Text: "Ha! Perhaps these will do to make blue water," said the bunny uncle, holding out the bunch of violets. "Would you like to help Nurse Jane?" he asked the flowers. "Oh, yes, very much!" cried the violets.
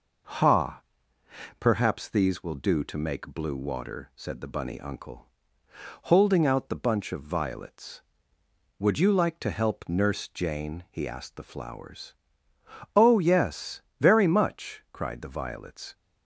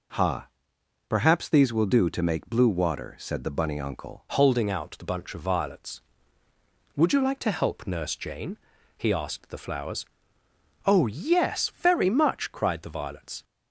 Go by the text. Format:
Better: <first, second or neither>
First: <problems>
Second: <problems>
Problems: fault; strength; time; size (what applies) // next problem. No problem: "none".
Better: first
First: none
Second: changes voice at "holding"; from 4.2 s on; 9.2 s long